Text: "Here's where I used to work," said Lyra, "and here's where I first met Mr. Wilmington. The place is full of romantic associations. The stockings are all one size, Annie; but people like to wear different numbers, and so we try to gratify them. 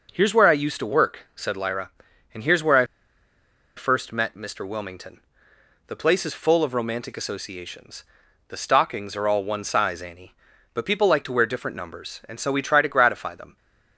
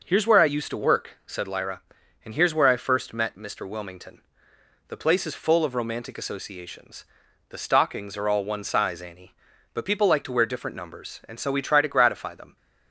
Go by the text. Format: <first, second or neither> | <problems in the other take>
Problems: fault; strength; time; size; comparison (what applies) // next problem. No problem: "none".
second | pauses between "I" and "first"; noticeable; at 2.8 s; 0.90 s long